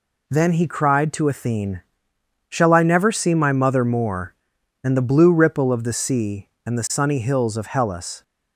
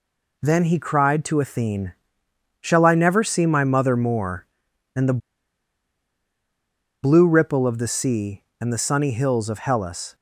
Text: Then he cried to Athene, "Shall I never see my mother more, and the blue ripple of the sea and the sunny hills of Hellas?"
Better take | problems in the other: first | pauses between "the" and "blue"; strong; at 5.1 s; 1.8 s long

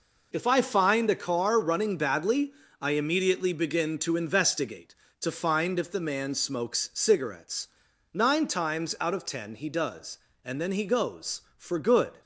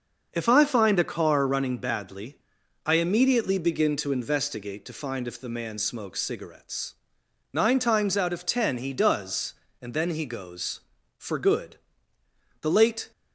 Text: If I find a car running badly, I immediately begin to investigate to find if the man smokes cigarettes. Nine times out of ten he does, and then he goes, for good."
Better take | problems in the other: first | starts louder than the rest; until 1.3 s; 6 dB // goes on to say "The late"; from 12.6 s on; 0.50 s long

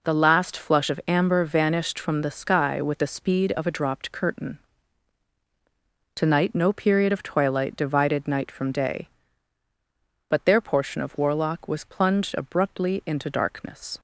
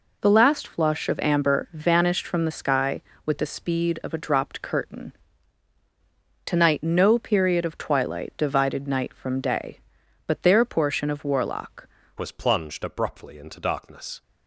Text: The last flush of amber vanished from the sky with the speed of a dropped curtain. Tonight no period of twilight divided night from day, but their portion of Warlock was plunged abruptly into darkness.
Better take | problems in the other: first | changes voice at "was"; from 12.1 s on; 2.1 s long

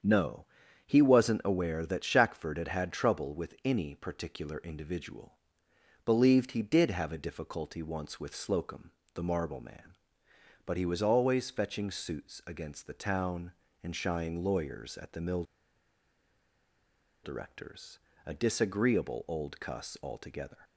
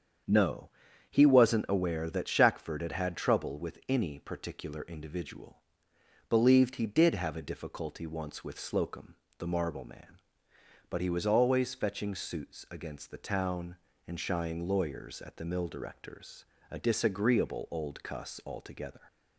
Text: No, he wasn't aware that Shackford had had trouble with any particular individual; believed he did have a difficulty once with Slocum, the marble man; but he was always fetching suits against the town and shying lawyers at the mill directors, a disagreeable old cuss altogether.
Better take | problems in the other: second | starts louder than the rest; strong; until 1.4 s; 7.5 dB; strong in the second // pauses between "mill" and "directors"; strong; at 15.4 s; 1.8 s long

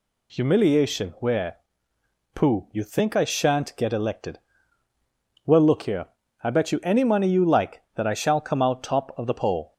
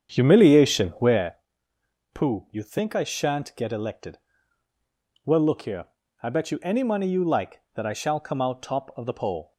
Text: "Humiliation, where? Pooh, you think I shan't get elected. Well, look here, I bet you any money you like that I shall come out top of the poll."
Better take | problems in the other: first | starts louder than the rest; strong; until 1.4 s; 8 dB

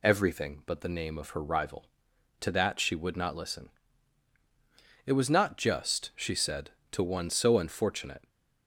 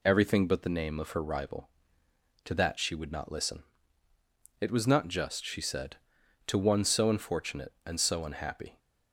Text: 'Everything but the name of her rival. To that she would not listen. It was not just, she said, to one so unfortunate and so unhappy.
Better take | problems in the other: second | stops before "and so unhappy"; at 8.2 s

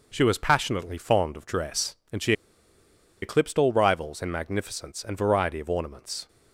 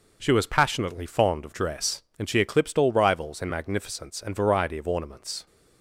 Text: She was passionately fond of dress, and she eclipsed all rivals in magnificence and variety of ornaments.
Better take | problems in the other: second | pauses between "she" and "eclipsed"; noticeable; at 2.3 s; 0.89 s long

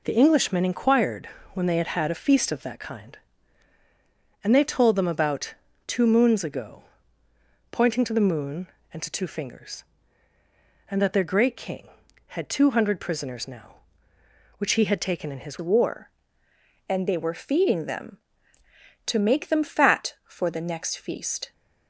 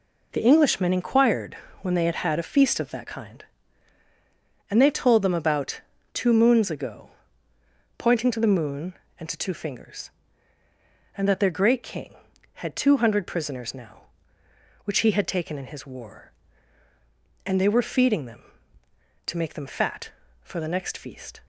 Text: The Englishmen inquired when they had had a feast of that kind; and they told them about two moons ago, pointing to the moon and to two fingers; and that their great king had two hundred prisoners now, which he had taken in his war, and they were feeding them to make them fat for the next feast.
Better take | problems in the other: second | pauses between "inquired" and "when"; slight; at 1.2 s; 0.24 s long; slight in the second // pauses between "about" and "two"; slight; at 5.5 s; 0.34 s long; slight in the second // changes voice at "war"; from 15.6 s on; 5.9 s long

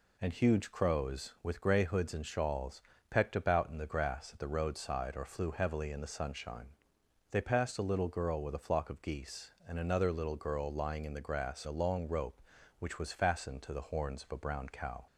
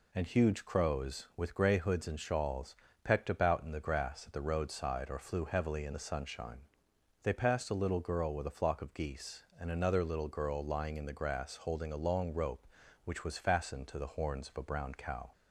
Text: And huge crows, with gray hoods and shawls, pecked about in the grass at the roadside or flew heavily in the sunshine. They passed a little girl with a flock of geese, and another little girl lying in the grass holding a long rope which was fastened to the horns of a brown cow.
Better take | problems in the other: second | skips "holding"; at 11.6 s

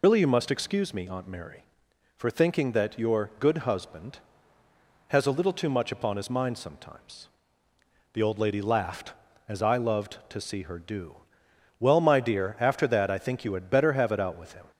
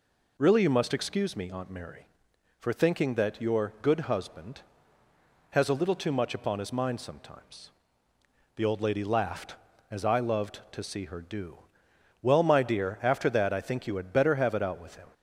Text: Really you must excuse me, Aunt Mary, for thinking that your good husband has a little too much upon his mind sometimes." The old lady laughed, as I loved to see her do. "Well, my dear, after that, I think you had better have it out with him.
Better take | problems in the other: second | loses the start of "Really"; at 0.0 s; 70 ms

